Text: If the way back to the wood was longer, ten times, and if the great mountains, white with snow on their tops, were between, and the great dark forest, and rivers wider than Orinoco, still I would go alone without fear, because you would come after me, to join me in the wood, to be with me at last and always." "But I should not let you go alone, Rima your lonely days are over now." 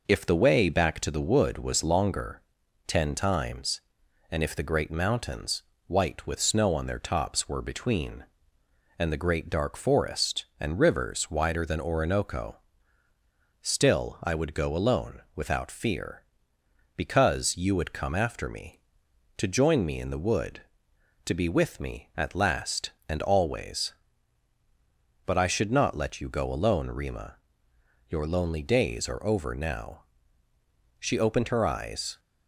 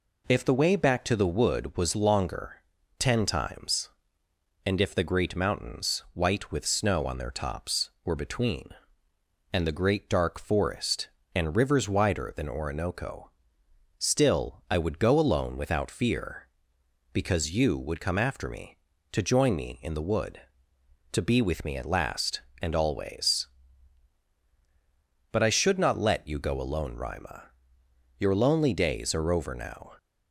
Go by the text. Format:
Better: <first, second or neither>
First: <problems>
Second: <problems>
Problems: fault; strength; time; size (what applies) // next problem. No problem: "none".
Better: second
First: pauses between "alone" and "without"; slight; at 15.2 s; 0.16 s long // pauses between "Rima" and "your"; noticeable; at 27.3 s; 0.72 s long // goes on to say "She opened her eyes"; noticeable; from 30.9 s on; 1.2 s long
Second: pauses between "Rima" and "your"; noticeable; at 27.5 s; 0.66 s long